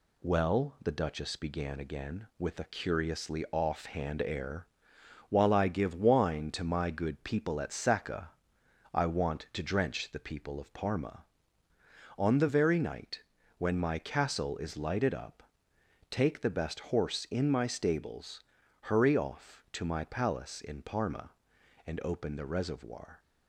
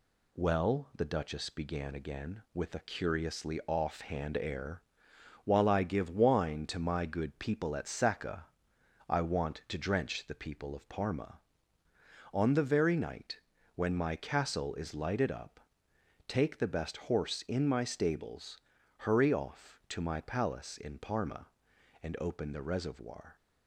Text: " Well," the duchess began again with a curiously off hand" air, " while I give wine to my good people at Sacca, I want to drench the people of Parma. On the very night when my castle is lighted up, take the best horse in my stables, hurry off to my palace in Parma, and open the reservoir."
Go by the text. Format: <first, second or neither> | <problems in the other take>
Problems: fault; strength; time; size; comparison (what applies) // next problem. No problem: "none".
neither | pauses between "night" and "when"; slight; the same in both